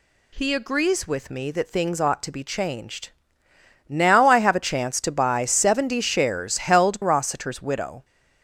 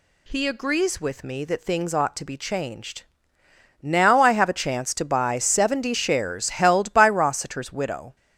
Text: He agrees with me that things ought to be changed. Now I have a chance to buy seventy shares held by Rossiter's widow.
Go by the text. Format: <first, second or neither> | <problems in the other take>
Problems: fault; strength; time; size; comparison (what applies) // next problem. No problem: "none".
second | skips "by"; at 7.0 s